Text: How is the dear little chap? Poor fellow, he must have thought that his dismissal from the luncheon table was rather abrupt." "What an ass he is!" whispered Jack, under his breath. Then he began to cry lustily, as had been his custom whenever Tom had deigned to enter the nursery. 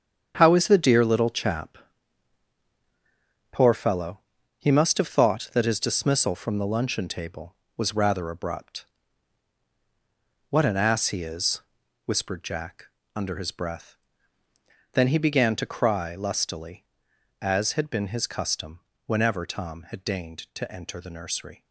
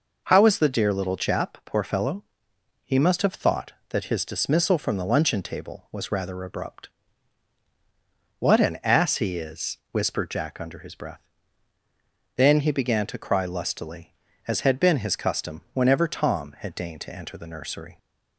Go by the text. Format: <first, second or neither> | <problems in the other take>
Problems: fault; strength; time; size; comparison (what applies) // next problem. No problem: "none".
second | gets quieter; strong; throughout; 10.5 dB // pauses between "custom" and "whenever"; slight; at 18.7 s; 0.26 s long